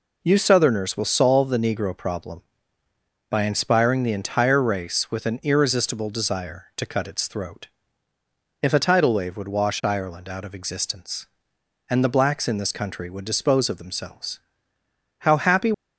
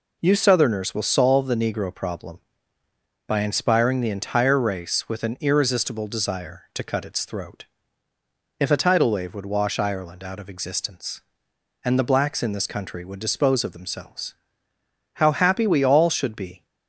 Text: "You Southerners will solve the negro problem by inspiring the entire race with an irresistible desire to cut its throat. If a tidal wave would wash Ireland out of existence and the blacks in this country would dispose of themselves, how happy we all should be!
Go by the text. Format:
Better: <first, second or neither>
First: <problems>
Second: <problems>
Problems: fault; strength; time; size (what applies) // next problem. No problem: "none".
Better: second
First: stops before "we all should be"; at 15.7 s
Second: none